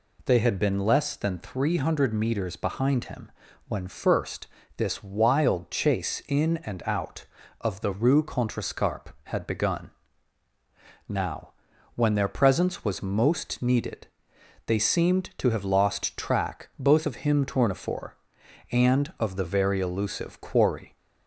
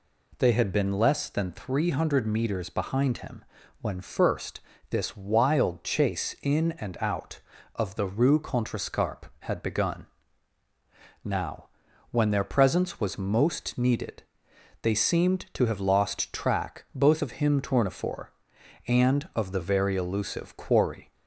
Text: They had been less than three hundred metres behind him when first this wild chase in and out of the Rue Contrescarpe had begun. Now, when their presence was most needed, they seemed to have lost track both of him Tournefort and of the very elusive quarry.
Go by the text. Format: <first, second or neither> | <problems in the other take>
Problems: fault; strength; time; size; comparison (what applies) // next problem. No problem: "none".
neither | pauses between "him" and "when"; the same in both // pauses between "first" and "this"; slight; the same in both